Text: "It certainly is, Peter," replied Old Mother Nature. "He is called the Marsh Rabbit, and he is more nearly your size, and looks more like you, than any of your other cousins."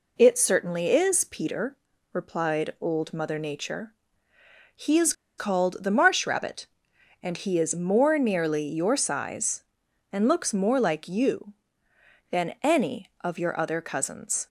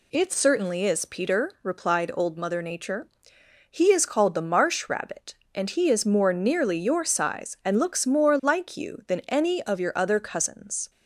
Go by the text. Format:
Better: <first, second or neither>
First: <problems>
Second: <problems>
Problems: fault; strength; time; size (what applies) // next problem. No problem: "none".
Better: second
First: pauses between "is" and "called"; slight; at 5.1 s; 0.25 s long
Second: none